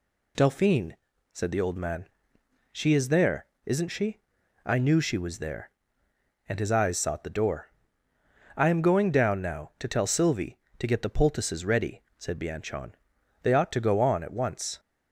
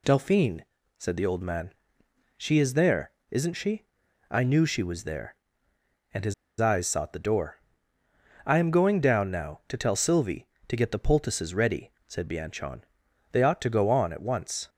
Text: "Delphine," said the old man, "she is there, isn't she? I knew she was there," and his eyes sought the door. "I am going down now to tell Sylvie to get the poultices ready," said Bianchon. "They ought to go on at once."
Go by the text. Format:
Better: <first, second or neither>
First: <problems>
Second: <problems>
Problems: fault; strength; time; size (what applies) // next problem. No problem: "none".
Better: first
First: none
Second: pauses between "his" and "eyes"; slight; at 6.3 s; 0.26 s long